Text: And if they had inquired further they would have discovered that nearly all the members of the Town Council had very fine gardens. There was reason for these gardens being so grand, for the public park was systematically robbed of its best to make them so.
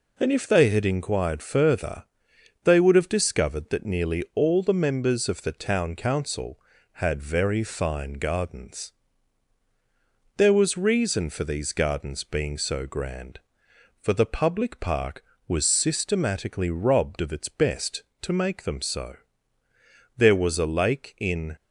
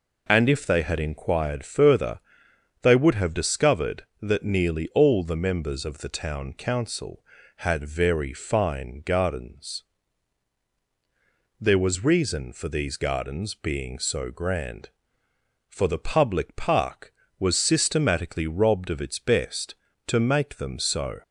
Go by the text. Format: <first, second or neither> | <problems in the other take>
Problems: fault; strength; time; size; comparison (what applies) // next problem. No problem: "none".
second | pauses between "further" and "they"; noticeable; at 2.0 s; 0.60 s long; noticeable in the second // goes on to say "There was a lake in"; from 20.1 s on; 1.3 s long